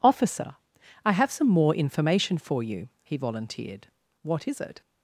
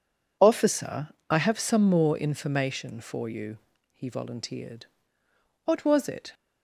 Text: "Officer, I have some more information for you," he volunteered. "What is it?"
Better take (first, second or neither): first